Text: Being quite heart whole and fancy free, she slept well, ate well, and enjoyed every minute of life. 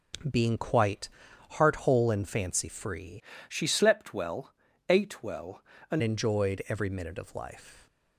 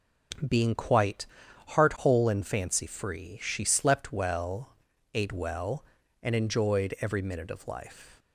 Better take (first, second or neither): second